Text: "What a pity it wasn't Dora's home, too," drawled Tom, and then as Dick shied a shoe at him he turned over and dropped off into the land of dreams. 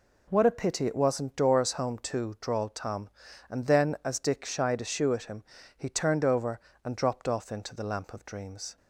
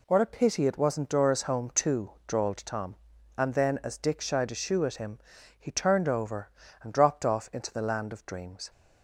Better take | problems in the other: second | pauses between "him" and "he"; slight; at 5.4 s; 0.32 s long; also in the second // says "lamp" for "land"; at 7.8 s

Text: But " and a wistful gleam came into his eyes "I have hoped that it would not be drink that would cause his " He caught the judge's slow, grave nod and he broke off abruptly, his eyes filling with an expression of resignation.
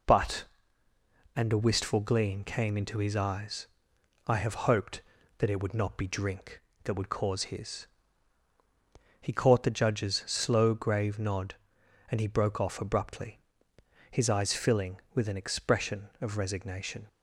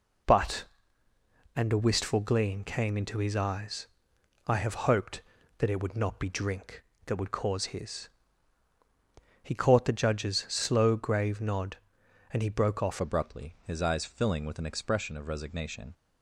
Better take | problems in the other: first | pauses between "eyes" and "I"; noticeable; at 3.8 s; 0.58 s long; noticeable in the first // changes voice at "abruptly"; from 12.9 s on; 3.0 s long

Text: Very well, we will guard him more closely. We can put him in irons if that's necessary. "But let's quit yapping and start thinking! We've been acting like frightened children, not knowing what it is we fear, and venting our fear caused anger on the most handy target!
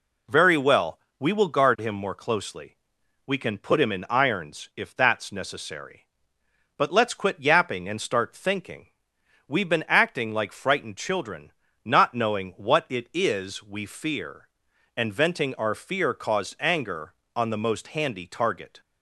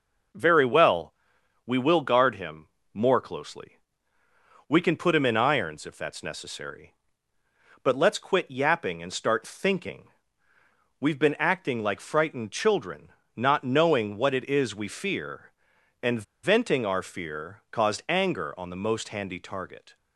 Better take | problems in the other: first | pauses between "him" and "more"; slight; at 2.6 s; 0.26 s long // pauses between "and" and "venting"; slight; at 16.2 s; 0.21 s long

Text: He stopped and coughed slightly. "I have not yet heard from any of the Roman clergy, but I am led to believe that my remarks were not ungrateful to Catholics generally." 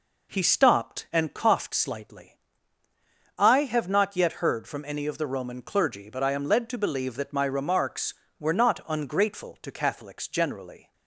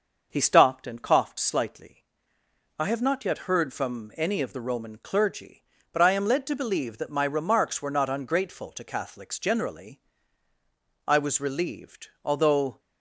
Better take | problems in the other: first | starts louder than the rest; until 1.3 s; 6.5 dB // goes on to say "I was relieved although"; strong; from 11.0 s on; 1.7 s long

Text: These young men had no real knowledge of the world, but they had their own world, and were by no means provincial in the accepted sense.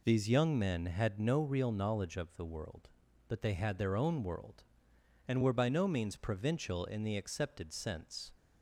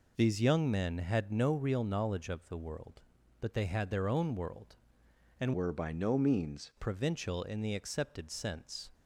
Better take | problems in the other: first | changes voice from "were" to "means"; from 5.5 to 6.7 s; 1.2 s long

